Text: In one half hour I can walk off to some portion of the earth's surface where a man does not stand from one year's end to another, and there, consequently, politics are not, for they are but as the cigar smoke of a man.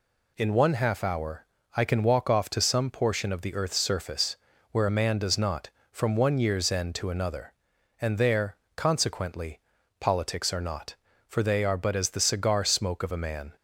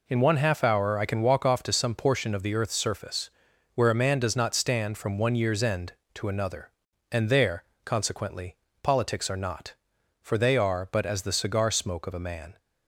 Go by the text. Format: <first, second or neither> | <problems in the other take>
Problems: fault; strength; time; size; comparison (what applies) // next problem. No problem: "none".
second | pauses between "hour" and "I"; slight; at 1.4 s; 0.30 s long // pauses between "surface" and "where"; slight; at 4.3 s; 0.36 s long; noticeable in the second // skips "stand"; at 5.7 s